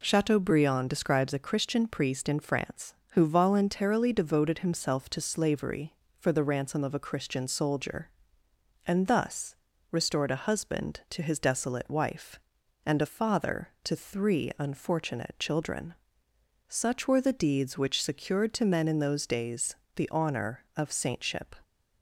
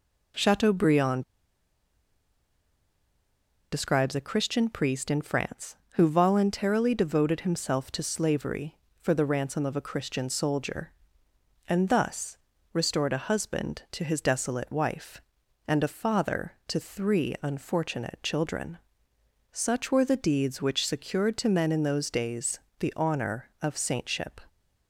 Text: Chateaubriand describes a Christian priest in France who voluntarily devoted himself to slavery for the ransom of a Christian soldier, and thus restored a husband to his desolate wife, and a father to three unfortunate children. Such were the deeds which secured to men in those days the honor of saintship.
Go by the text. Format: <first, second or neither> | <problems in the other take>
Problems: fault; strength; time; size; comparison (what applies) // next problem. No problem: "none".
first | pauses between "Chateaubriand" and "describes"; strong; at 1.2 s; 2.4 s long // pauses between "thus" and "restored"; at 12.3 s; 0.38 s long; also in the first // pauses between "days" and "the"; slight; at 22.5 s; 0.20 s long; slight in the first